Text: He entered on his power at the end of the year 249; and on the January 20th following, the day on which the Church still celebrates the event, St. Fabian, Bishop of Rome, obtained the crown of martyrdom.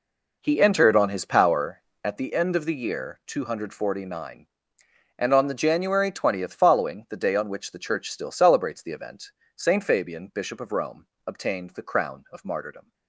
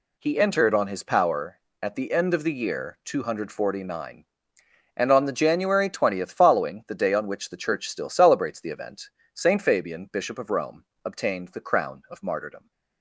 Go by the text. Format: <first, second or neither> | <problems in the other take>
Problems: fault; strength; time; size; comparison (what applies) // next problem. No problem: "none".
second | starts louder than the rest; noticeable; until 2.3 s; 4.5 dB